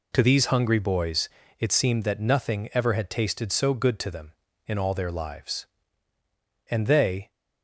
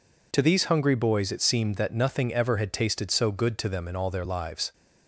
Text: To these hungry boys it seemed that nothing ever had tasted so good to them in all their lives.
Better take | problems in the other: second | pauses between "boys" and "it"; slight; at 1.2 s; 0.32 s long // goes on to say "And they"; noticeable; from 6.6 s on; 0.62 s long

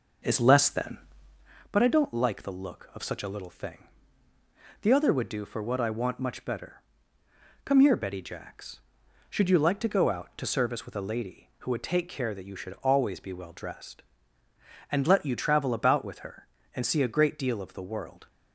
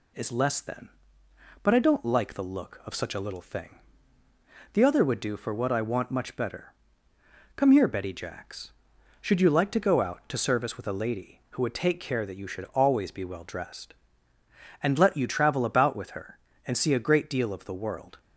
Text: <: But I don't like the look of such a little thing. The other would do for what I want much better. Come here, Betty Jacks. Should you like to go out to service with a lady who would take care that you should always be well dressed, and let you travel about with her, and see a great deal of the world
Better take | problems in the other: second | starts louder than the rest; noticeable; until 1.6 s; 6 dB

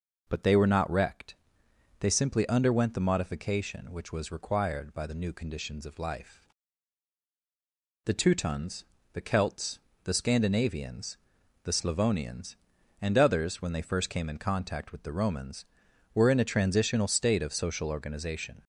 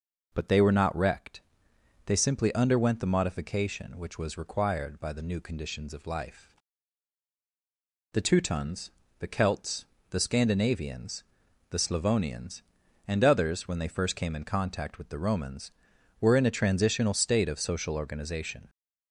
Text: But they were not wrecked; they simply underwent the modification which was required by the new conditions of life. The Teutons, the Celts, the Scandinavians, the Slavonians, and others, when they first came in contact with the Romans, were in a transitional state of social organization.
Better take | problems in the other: neither | none

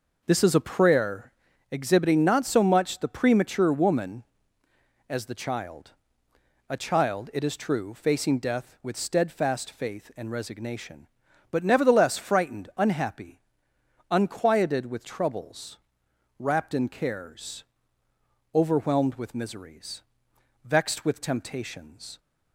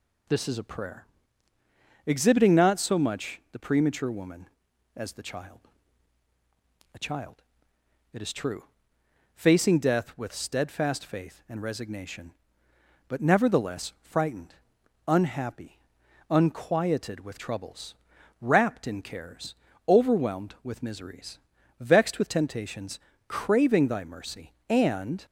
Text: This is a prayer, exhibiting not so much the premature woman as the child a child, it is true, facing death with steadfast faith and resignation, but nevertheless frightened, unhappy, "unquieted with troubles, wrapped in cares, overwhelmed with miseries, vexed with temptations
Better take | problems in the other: first | pauses between "child" and "a"; strong; at 5.5 s; 1.3 s long; noticeable in the first // goes on to say "craving Thy mercy and"; strong; from 23.2 s on; 1.9 s long

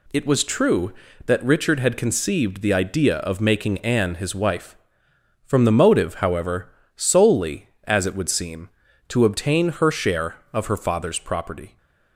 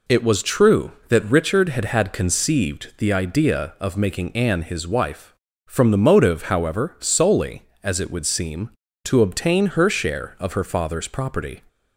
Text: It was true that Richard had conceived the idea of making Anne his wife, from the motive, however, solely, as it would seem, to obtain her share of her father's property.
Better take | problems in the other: first | says "had" twice; at 1.8 s

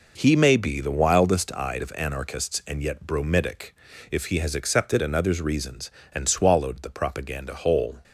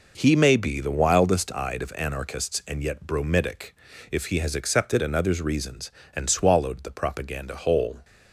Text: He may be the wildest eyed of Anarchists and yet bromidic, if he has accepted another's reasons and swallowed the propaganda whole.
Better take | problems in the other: neither | none

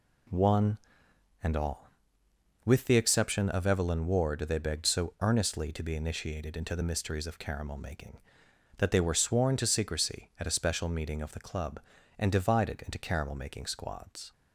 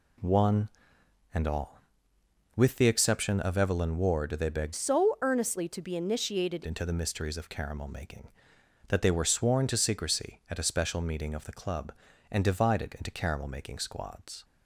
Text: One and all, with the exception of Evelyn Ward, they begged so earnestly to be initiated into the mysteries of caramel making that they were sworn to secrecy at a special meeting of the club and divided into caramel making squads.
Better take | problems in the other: first | changes voice from "so" to "initiated"; from 4.7 to 6.6 s; 1.9 s long

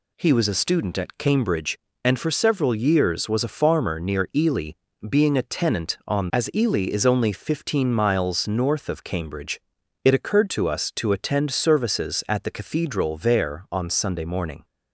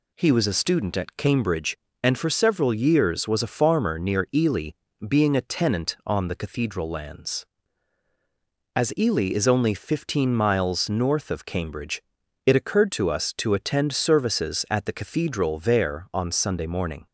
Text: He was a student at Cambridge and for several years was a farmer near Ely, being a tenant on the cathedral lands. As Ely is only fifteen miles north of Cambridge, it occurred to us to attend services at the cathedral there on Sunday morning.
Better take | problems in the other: second | skips "the cathedral lands"; at 6.3 s

